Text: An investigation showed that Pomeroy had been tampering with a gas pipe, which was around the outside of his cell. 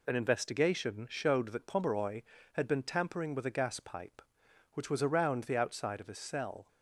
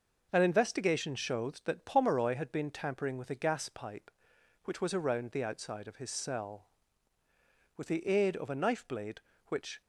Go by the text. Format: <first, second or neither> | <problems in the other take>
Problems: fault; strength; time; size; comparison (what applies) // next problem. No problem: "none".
first | goes on to say "With the aid of a knife blade which"; strong; from 7.7 s on; 2.0 s long